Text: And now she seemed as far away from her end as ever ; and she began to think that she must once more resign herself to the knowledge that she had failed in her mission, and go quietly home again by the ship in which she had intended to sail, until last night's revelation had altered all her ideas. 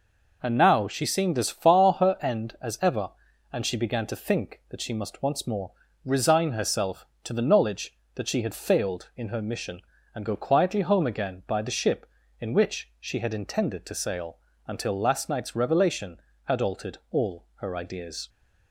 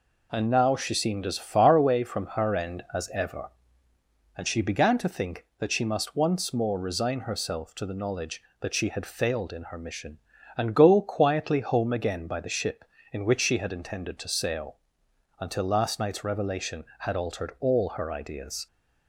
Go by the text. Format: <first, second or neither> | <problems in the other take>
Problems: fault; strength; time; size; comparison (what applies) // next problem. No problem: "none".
second | skips "away from"; at 1.9 s // pauses between "more" and "resign"; slight; at 5.7 s; 0.34 s long